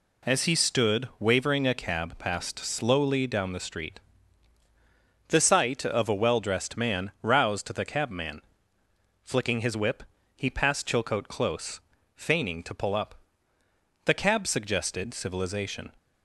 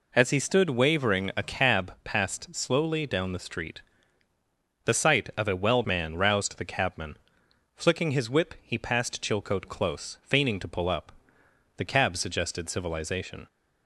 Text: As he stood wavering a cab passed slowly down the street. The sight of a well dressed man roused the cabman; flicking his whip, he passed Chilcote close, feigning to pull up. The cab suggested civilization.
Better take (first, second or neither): first